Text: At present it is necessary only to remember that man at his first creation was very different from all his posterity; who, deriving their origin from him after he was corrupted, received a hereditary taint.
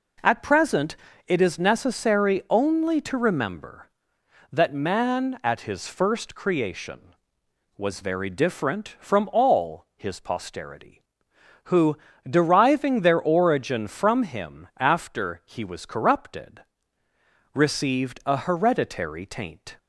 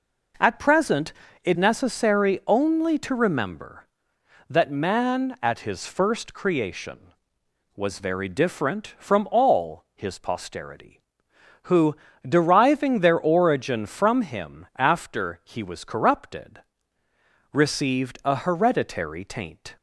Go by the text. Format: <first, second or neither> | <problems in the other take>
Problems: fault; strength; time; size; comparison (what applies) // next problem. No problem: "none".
first | pauses between "present" and "it"; slight; at 1.1 s; 0.32 s long; slight in the first // skips "is"; at 1.5 s